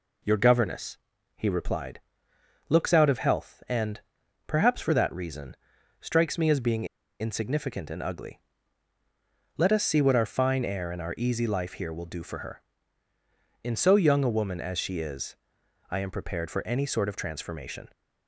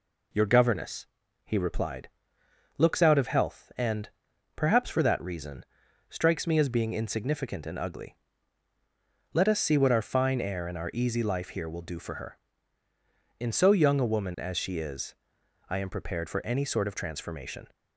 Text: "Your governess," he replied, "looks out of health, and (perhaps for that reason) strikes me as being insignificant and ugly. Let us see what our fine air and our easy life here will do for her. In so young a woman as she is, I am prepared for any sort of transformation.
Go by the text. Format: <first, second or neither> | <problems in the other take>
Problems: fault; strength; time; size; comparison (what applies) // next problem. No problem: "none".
second | pauses between "being" and "insignificant"; slight; at 6.8 s; 0.34 s long